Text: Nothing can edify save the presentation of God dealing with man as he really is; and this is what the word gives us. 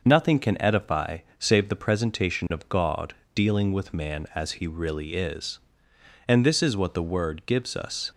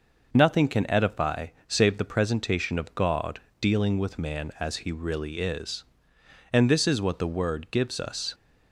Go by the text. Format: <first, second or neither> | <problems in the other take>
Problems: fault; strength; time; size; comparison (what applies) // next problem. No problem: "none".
neither | pauses between "edify" and "save"; slight; the same in both // pauses between "God" and "dealing"; slight; the same in both